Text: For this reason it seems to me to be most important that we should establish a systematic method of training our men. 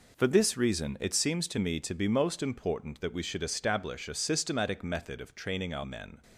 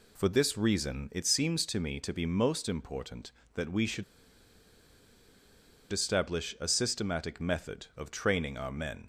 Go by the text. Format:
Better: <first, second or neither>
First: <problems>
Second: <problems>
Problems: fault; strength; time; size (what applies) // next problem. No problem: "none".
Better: first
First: none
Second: pauses between "should" and "establish"; strong; at 4.0 s; 1.8 s long